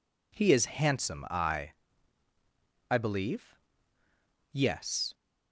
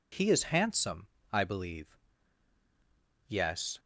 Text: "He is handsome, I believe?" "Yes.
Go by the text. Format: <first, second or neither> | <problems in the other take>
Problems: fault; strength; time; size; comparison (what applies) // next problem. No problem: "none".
second | says "I" twice; at 2.8 s